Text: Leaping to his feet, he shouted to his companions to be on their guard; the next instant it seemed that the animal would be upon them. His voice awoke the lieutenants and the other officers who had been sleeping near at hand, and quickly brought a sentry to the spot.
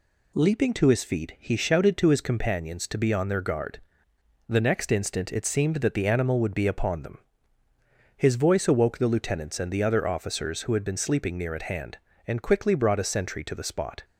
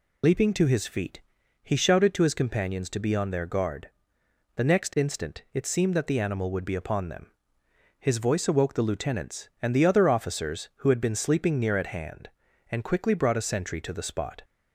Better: first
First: none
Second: loses the start of "Leaping"; at 0.2 s; 50 ms

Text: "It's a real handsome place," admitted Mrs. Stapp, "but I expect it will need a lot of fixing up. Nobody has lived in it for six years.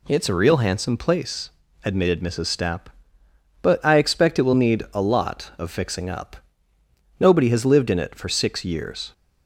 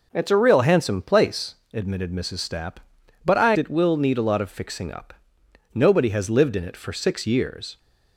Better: first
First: none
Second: skips "expect"; at 3.5 s

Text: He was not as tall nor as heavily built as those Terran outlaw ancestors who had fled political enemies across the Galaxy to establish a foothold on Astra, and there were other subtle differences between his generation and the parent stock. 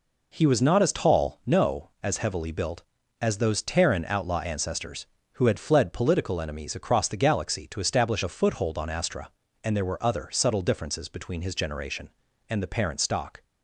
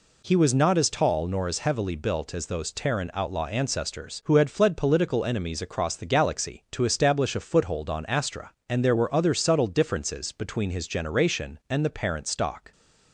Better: second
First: says "no" for "nor"; at 1.4 s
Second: none

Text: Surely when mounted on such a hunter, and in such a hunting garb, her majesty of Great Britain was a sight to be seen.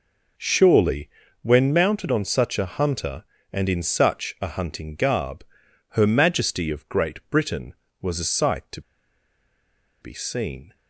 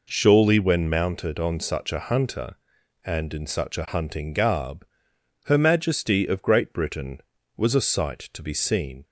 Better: second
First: pauses between "Surely" and "when"; slight; at 1.0 s; 0.34 s long // pauses between "to" and "be"; at 8.8 s; 1.2 s long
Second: none

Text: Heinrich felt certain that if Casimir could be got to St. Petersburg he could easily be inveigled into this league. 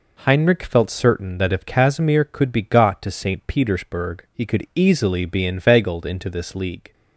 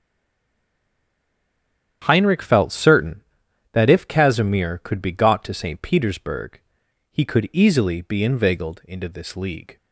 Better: first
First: none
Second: stays silent before the first word; noticeable; until 2.0 s; 2.0 s long // starts louder than the rest; strong; until 3.0 s; 9.5 dB // pauses between "Petersburg" and "he"; noticeable; at 6.5 s; 0.54 s long

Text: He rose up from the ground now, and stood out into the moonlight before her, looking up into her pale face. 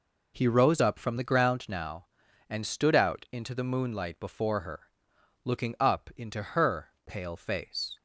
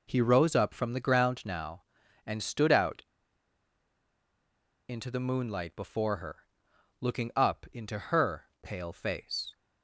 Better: first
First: pauses between "her" and "pale"; slight; at 6.8 s; 0.18 s long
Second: pauses between "out" and "into"; strong; at 3.0 s; 1.8 s long // pauses between "her" and "pale"; slight; at 8.4 s; 0.18 s long

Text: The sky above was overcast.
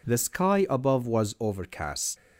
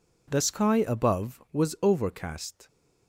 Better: neither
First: none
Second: none

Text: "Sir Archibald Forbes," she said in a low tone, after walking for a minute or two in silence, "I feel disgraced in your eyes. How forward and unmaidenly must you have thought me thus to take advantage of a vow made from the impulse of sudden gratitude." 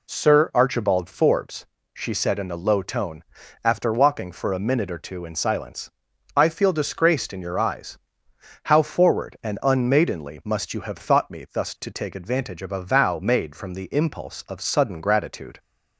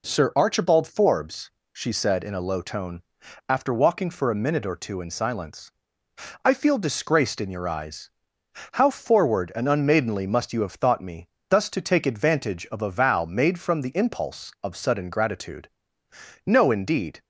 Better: first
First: none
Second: pauses between "me" and "thus"; slight; at 11.3 s; 0.18 s long // goes on to say "No indeed"; noticeable; from 16.4 s on; 0.78 s long

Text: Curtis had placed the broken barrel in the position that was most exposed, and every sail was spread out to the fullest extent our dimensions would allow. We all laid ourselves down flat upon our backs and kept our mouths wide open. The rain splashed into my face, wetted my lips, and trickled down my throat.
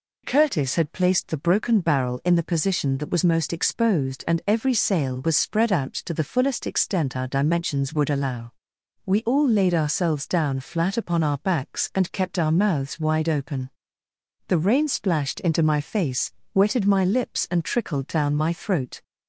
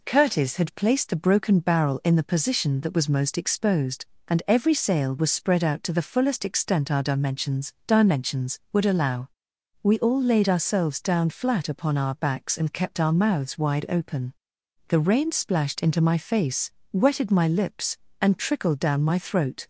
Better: first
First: none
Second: says "dimensions" twice; at 7.8 s

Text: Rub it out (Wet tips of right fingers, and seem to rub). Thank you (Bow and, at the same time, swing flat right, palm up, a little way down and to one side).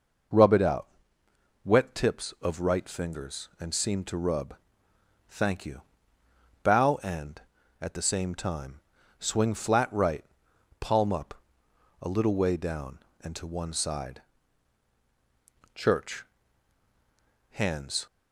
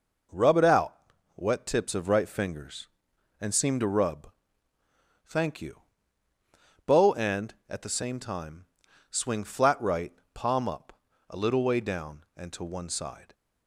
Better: second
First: goes on to say "Church Hands"; strong; from 15.7 s on; 2.3 s long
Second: none

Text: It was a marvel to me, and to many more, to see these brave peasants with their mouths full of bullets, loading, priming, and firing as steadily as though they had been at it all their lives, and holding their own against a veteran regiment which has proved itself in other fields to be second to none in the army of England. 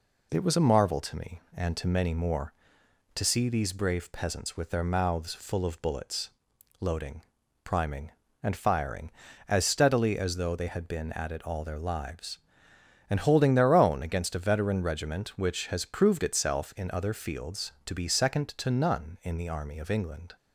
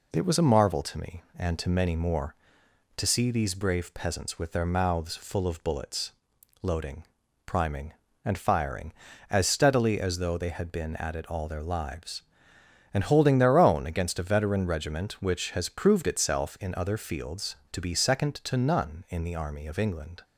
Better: neither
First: none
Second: none

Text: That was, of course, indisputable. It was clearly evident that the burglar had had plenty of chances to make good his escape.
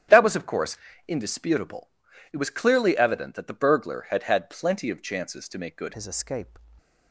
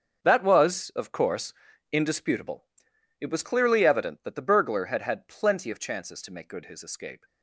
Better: second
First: starts louder than the rest; strong; until 1.4 s; 10 dB // changes voice at "his"; from 5.9 s on; 0.6 s long // stays silent after the last word; slight; from 6.5 s on; 0.6 s long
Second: starts louder than the rest; until 1.2 s; 7 dB

